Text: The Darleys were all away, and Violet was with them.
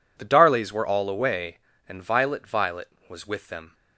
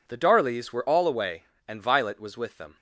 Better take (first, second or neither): second